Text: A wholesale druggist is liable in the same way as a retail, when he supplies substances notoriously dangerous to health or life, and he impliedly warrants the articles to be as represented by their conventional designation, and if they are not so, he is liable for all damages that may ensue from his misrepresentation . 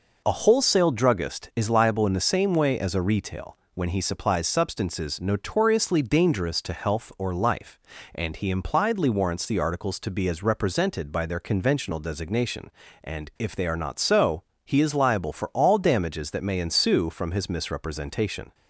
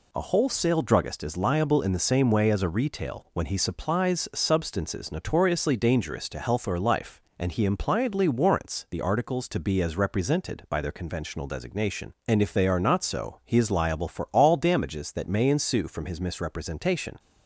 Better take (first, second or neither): neither